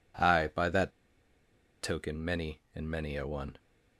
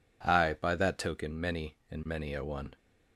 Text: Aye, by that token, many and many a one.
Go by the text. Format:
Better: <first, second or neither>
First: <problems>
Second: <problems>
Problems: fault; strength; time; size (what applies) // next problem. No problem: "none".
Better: second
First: pauses between "that" and "token"; noticeable; at 0.9 s; 0.92 s long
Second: none